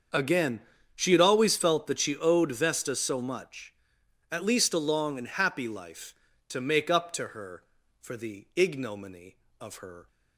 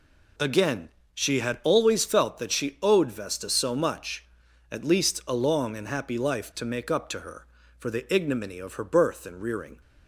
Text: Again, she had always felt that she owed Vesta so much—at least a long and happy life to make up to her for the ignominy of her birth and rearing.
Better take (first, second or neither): second